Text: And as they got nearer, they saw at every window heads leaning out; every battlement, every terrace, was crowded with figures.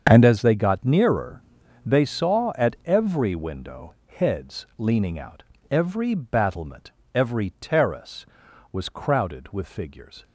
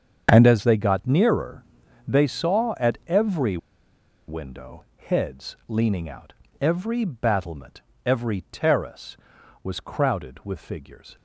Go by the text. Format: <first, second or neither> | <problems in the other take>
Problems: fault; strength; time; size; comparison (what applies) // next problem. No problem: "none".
first | starts louder than the rest; until 1.3 s; 7 dB; strong in the first // pauses between "every" and "window"; noticeable; at 3.5 s; 0.70 s long